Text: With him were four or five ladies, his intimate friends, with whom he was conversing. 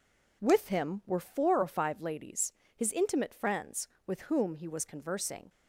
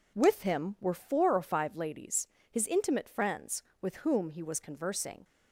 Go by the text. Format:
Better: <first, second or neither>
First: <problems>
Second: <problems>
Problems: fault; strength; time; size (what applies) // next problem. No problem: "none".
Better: neither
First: none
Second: none